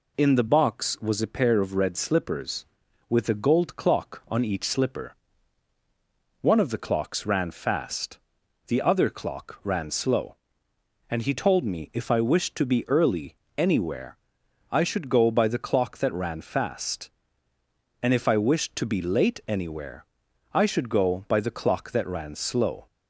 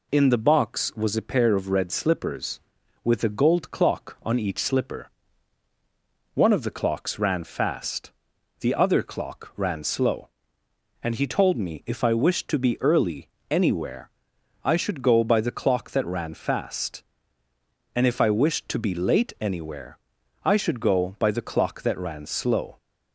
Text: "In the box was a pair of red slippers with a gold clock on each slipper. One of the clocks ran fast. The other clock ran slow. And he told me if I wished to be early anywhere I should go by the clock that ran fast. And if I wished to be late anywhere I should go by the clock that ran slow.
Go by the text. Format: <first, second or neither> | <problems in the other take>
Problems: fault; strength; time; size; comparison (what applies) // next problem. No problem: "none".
neither | pauses between "early" and "anywhere"; slight; the same in both // pauses between "anywhere" and "I"; noticeable; the same in both // pauses between "anywhere" and "I"; noticeable; the same in both